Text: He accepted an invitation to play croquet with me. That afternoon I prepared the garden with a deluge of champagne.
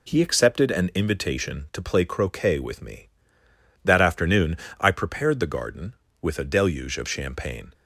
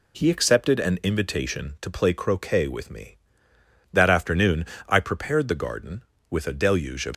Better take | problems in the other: first | pauses between "afternoon" and "I"; slight; at 4.6 s; 0.24 s long; slight in the first // stops before "champagne"; at 7.1 s

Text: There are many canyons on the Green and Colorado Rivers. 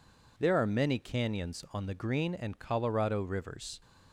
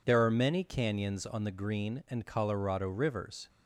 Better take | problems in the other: neither | none

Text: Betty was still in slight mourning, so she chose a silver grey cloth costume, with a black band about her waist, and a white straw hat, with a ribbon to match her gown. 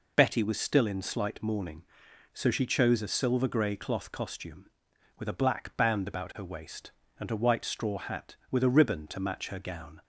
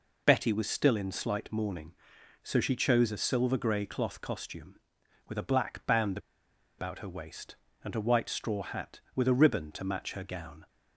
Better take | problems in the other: first | pauses between "band" and "about"; noticeable; at 6.1 s; 0.60 s long

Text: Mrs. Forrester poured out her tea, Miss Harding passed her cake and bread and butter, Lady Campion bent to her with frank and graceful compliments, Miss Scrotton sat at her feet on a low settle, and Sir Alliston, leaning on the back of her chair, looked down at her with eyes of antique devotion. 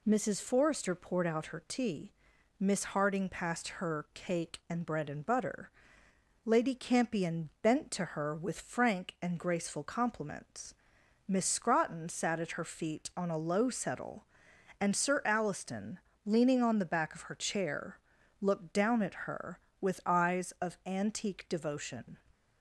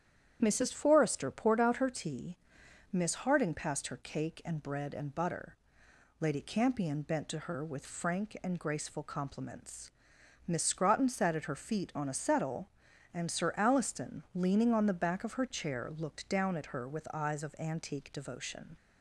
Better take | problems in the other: first | starts louder than the rest; strong; until 1.4 s; 9.5 dB // skips "low"; at 12.1 s

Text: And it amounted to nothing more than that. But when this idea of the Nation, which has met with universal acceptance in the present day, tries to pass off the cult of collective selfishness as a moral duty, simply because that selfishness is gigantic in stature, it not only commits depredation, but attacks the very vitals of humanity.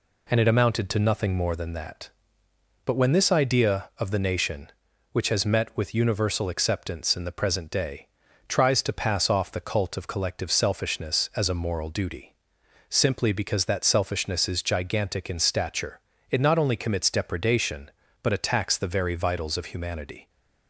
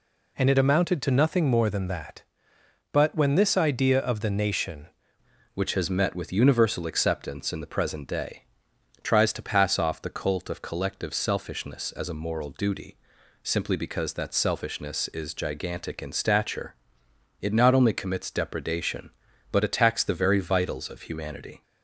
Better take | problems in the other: first | changes voice at "which"; from 5.5 s on; 16.1 s long

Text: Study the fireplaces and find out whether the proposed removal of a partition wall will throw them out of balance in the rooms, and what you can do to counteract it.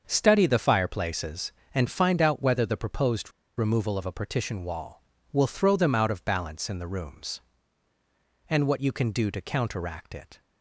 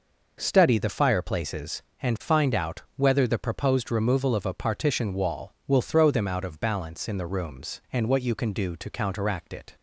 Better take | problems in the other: second | starts louder than the rest; until 1.0 s; 6.5 dB // pauses between "proposed" and "removal"; slight; at 3.3 s; 0.27 s long

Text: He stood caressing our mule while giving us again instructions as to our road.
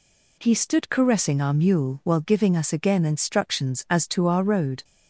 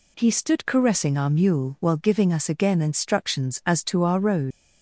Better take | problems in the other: first | leaves "road" unfinished; at 4.5 s; 95 ms

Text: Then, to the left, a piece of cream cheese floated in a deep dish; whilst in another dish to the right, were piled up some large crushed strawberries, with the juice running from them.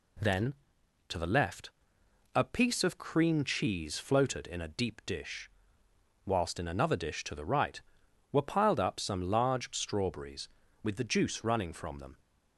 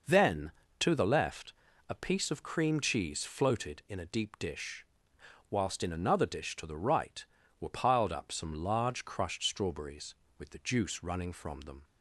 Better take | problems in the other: second | skips "crushed"; at 9.7 s

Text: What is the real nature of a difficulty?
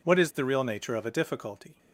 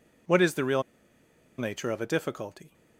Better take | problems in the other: first | pauses between "real" and "nature"; noticeable; at 0.8 s; 0.76 s long

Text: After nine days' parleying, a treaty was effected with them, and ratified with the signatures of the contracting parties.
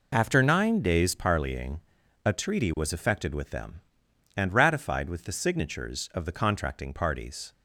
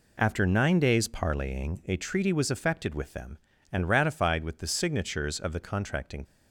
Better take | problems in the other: first | stops before "parties"; at 6.2 s

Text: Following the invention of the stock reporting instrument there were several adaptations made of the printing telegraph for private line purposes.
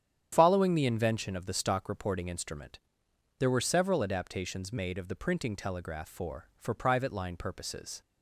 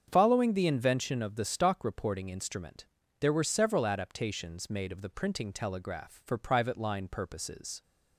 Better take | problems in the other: second | starts louder than the rest; strong; until 1.3 s; 9 dB; strong in the second // pauses between "instrument" and "there"; noticeable; at 2.7 s; 0.58 s long; slight in the second // says "for" twice; at 6.5 s

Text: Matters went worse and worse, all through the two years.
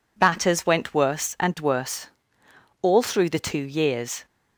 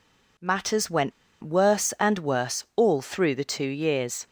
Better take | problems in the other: first | pauses between "went" and "worse"; slight; at 1.1 s; 0.31 s long

